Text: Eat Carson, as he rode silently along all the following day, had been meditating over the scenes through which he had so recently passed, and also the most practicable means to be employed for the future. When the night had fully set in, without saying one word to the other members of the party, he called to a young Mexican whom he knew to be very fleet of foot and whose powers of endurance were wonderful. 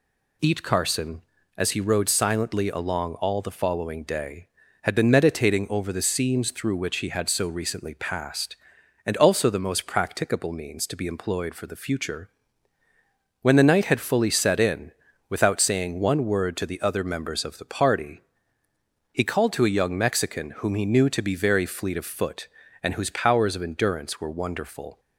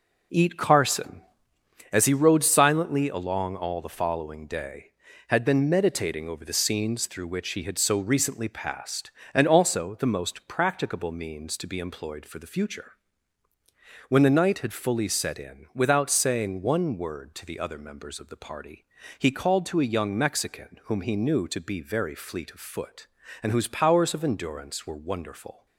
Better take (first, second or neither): first